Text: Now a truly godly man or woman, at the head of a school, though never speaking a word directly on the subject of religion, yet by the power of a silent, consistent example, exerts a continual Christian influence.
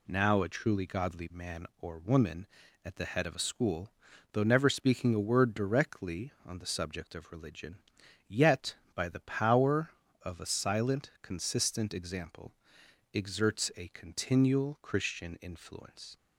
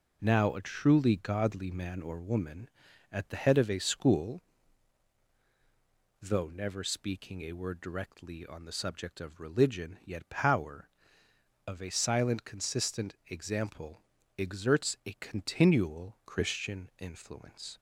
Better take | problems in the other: first | skips "by the"; at 10.2 s

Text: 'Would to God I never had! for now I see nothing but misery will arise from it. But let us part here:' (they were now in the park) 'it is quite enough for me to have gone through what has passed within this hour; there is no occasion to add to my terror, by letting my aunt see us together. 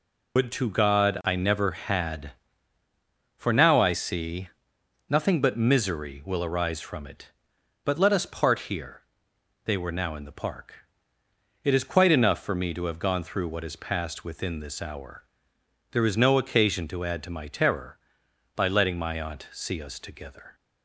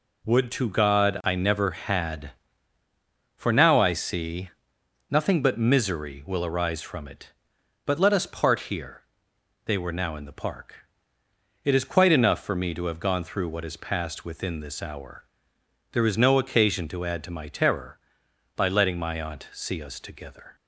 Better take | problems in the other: second | loses the start of "Would"; at 0.3 s; 105 ms // pauses between "see" and "nothing"; noticeable; at 4.4 s; 0.62 s long; noticeable in the second

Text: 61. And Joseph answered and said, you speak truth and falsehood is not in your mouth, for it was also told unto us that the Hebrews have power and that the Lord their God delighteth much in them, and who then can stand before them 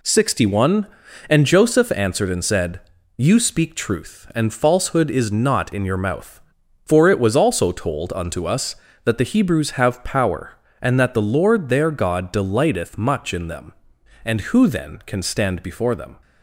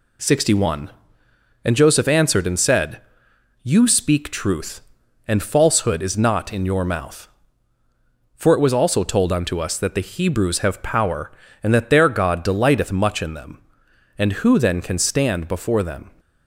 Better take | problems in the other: first | skips "the Lord"; at 11.8 s

